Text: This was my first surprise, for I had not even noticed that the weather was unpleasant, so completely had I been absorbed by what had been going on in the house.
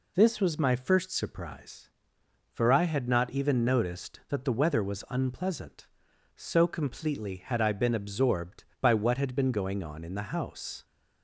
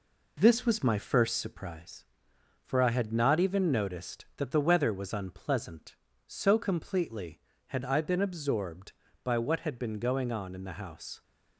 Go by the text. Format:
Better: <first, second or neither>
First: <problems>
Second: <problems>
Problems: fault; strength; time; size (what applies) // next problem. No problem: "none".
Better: first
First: none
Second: gets quieter; throughout; 4 dB